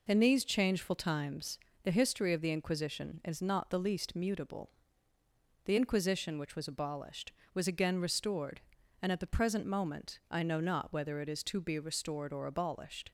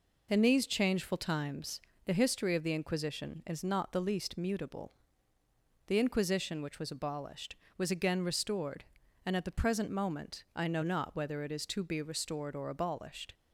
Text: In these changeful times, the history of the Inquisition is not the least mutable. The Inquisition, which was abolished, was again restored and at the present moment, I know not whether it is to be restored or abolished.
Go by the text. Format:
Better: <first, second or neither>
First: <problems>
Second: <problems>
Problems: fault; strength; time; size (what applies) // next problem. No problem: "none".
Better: neither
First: none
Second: none